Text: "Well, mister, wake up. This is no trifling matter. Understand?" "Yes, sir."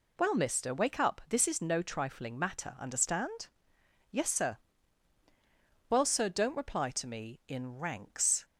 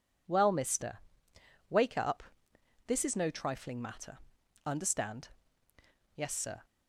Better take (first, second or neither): second